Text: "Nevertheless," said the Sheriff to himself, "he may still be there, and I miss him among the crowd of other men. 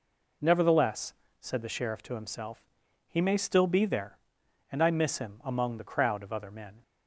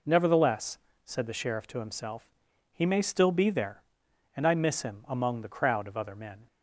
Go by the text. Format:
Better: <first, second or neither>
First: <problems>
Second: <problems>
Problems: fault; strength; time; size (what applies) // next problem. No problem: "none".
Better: neither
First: none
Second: none